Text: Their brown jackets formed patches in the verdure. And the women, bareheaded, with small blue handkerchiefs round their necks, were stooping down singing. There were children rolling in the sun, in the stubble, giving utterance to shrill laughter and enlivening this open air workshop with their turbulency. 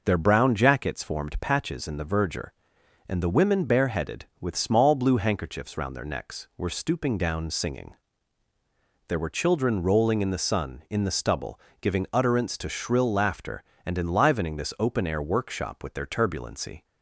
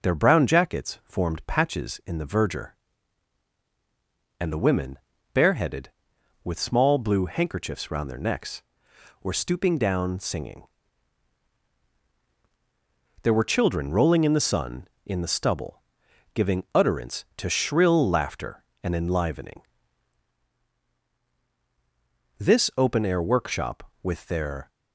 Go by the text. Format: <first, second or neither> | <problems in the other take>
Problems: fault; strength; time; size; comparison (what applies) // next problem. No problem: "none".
first | pauses between "enlivening" and "this"; strong; at 19.6 s; 2.7 s long // stops before "turbulency"; at 24.6 s